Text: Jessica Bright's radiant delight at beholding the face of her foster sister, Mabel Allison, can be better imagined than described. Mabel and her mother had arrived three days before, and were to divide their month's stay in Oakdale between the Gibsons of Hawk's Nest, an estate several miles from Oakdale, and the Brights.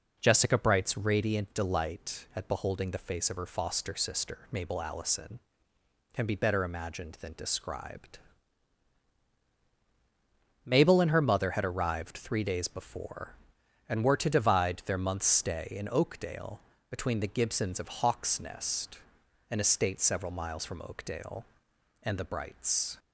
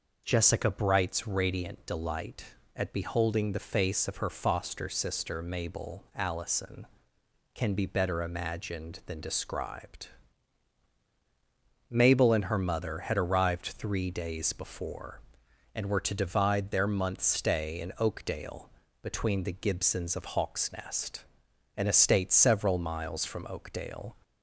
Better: first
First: pauses between "Oakdale" and "between"; slight; at 16.5 s; 0.30 s long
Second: pauses between "Oakdale" and "between"; slight; at 18.6 s; 0.32 s long // stops before "and the Brights"; at 24.2 s

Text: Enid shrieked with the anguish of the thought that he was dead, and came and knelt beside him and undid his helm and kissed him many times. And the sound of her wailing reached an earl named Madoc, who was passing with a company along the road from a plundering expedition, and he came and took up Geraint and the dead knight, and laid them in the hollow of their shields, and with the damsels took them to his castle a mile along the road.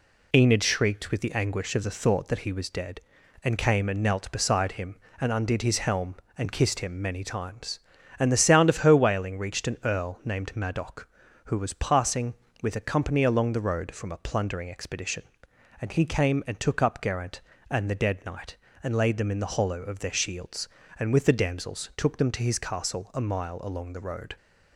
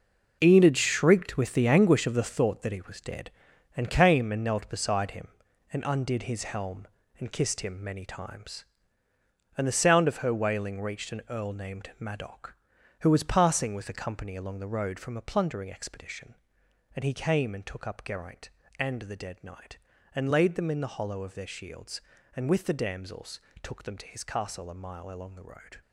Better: first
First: none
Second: gets quieter; strong; throughout; 11 dB // pauses between "damsels" and "took"; slight; at 23.4 s; 0.22 s long

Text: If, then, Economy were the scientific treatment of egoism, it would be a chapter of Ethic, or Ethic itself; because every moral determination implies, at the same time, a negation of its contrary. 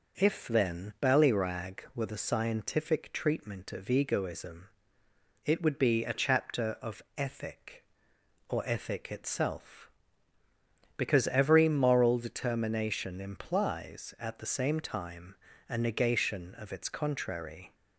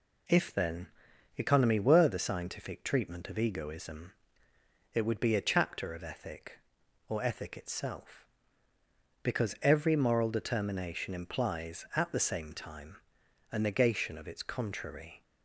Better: second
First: says "Ballyrag" for "Economy"; at 1.0 s // pauses between "of" and "Ethic"; slight; at 7.0 s; 0.16 s long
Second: none

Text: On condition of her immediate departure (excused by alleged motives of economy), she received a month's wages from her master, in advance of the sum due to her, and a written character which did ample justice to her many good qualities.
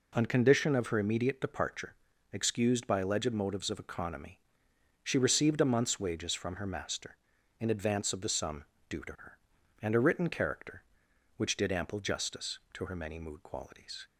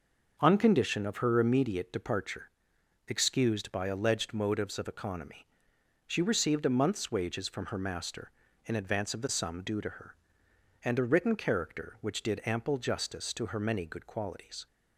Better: second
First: pauses between "sum" and "due"; slight; at 8.6 s; 0.26 s long // says "mood" for "good"; at 13.1 s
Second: none

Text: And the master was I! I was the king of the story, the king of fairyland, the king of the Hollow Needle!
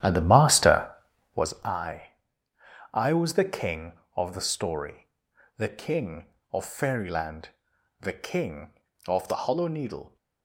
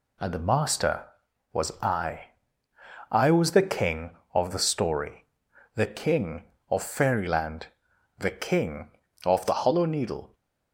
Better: second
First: starts louder than the rest; strong; until 1.5 s; 11.5 dB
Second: none

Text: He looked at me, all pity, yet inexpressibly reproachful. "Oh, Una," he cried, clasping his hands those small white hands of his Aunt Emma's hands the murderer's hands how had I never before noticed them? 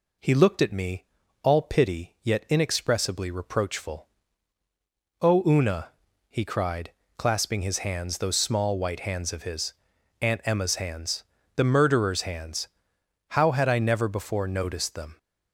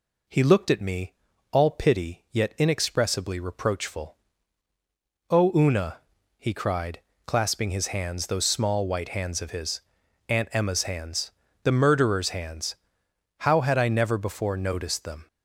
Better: neither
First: pauses between "his" and "Aunt"; noticeable; at 9.7 s; 0.46 s long // pauses between "hands" and "the"; slight; at 11.2 s; 0.32 s long // pauses between "hands" and "how"; noticeable; at 12.6 s; 0.64 s long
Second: pauses between "his" and "Aunt"; noticeable; at 9.8 s; 0.46 s long // pauses between "hands" and "the"; slight; at 11.3 s; 0.32 s long // pauses between "hands" and "how"; noticeable; at 12.7 s; 0.66 s long

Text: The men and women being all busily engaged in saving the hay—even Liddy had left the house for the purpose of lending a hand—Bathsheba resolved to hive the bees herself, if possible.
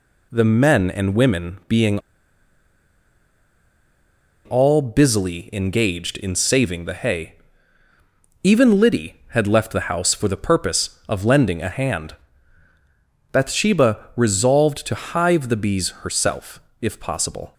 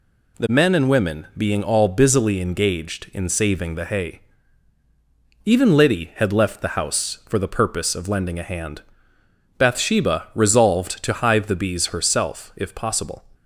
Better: second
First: pauses between "being" and "all"; strong; at 1.9 s; 2.4 s long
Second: none

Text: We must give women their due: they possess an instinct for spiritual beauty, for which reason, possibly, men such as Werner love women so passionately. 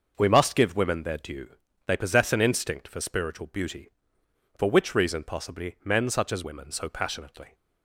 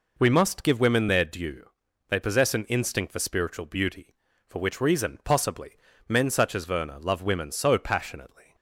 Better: second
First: starts louder than the rest; noticeable; until 1.1 s; 6 dB // skips "Werner love"; at 6.4 s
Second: none

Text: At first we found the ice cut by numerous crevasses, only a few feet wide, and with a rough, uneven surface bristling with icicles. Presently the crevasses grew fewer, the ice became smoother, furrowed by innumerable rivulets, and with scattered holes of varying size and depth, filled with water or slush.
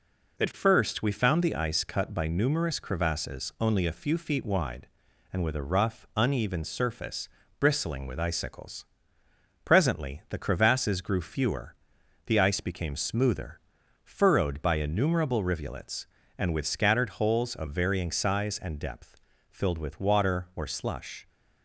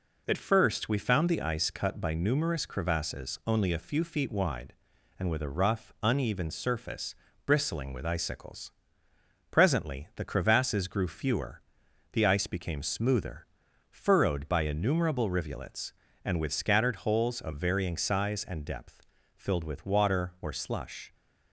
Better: neither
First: pauses between "surface" and "bristling"; slight; at 7.2 s; 0.30 s long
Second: pauses between "surface" and "bristling"; slight; at 7.1 s; 0.30 s long

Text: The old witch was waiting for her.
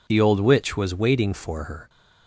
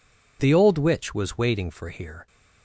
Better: first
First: none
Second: says "here" for "her"; at 1.9 s

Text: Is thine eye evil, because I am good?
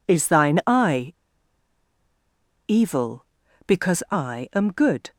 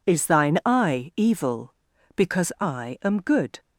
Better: second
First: pauses between "eye" and "evil"; strong; at 1.1 s; 1.5 s long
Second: none

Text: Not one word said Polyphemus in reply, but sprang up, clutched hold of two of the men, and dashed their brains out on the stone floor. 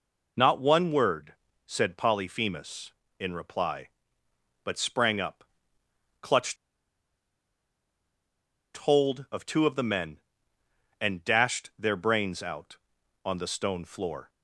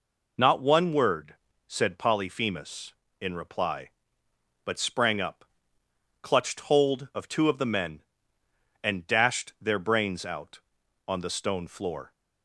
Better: second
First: pauses between "word" and "said"; slight; at 1.3 s; 0.34 s long // pauses between "clutched" and "hold"; strong; at 6.5 s; 2.2 s long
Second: pauses between "word" and "said"; slight; at 1.3 s; 0.34 s long

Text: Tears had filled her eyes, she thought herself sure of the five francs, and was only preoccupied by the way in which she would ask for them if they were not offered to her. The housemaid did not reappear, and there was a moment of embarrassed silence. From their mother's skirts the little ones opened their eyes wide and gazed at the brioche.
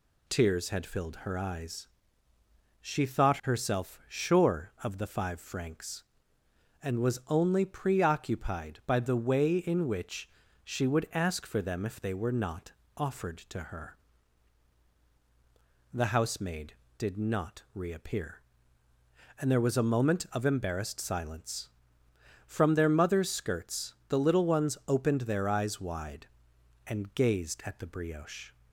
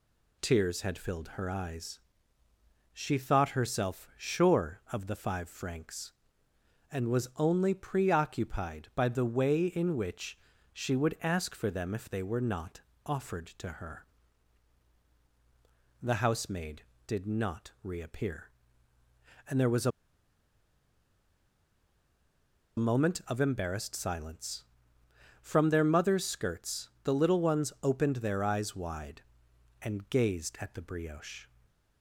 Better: first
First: pauses between "which" and "she"; slight; at 10.2 s; 0.36 s long // pauses between "not" and "offered"; slight; at 12.7 s; 0.24 s long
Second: pauses between "which" and "she"; slight; at 10.3 s; 0.36 s long // pauses between "not" and "offered"; slight; at 12.8 s; 0.24 s long // pauses between "a" and "moment"; strong; at 19.9 s; 2.8 s long

